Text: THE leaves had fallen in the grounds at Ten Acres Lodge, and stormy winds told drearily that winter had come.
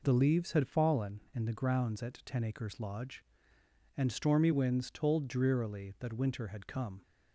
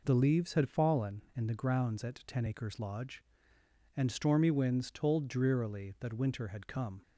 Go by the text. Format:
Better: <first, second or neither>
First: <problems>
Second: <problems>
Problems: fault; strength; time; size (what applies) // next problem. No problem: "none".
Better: neither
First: none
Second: none